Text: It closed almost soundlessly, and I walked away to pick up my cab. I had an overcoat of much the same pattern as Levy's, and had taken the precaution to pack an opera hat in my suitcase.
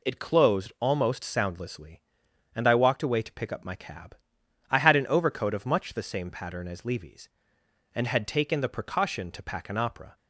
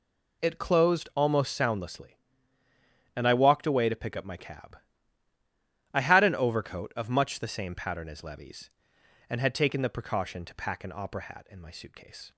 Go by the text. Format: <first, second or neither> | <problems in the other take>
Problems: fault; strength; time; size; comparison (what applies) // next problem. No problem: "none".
second | stops before "hat in my suitcase"; at 10.1 s